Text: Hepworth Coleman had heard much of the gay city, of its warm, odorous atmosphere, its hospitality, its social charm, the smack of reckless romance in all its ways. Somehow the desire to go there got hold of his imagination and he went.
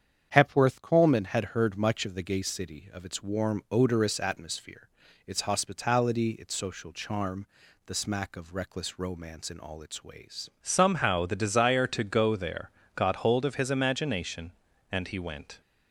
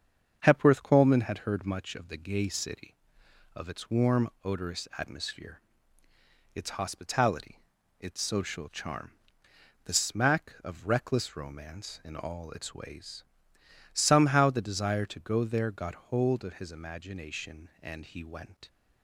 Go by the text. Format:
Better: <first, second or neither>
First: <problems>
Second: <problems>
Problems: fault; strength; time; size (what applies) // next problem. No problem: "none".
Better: second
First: starts louder than the rest; strong; until 1.3 s; 8 dB // changes voice at "Somehow"; from 10.6 s on; 5.0 s long // pauses between "there" and "got"; slight; at 12.7 s; 0.24 s long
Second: starts louder than the rest; strong; until 1.4 s; 7 dB